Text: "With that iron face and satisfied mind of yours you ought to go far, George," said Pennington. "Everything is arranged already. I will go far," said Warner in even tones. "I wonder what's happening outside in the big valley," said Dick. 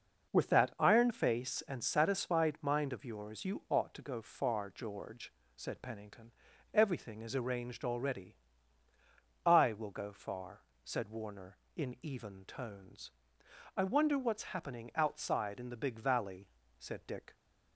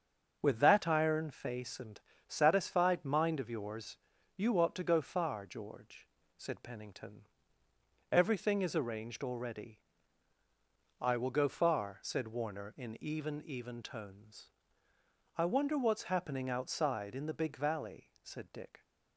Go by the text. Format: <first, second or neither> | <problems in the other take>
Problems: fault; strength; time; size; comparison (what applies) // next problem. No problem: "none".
first | starts louder than the rest; until 1.4 s; 7 dB // pauses between "and" and "satisfied"; slight; at 1.9 s; 0.28 s long // pauses between "yours" and "you"; at 3.9 s; 0.40 s long // says "even" twice; at 13.4 s